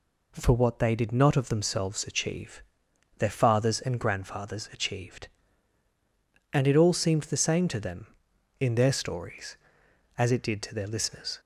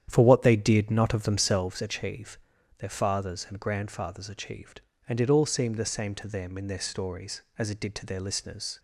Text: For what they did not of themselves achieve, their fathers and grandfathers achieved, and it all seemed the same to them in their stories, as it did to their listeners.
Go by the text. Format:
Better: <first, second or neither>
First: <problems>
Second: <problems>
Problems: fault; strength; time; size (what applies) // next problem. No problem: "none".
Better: first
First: none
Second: starts louder than the rest; strong; until 1.6 s; 9.5 dB